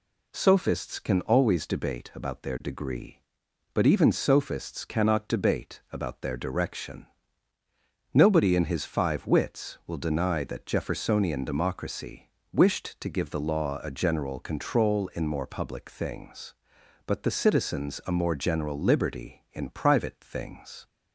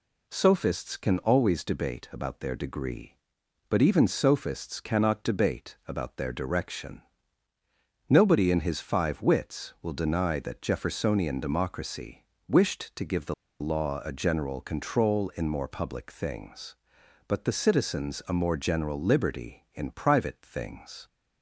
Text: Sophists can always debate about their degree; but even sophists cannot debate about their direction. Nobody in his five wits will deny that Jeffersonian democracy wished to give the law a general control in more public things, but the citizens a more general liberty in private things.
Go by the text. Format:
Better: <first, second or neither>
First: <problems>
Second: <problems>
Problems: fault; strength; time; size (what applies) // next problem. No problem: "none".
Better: first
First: pauses between "democracy" and "wished"; slight; at 12.3 s; 0.20 s long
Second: pauses between "democracy" and "wished"; slight; at 12.2 s; 0.20 s long // pauses between "the" and "law"; slight; at 13.3 s; 0.27 s long